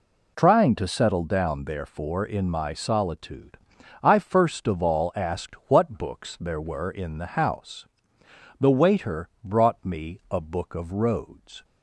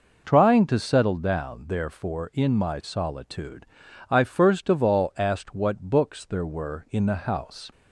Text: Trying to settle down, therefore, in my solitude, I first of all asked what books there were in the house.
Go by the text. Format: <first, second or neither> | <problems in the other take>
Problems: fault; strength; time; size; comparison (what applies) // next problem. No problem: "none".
second | goes on to say "The waiter brought me a Book of Roads"; strong; from 8.5 s on; 3.0 s long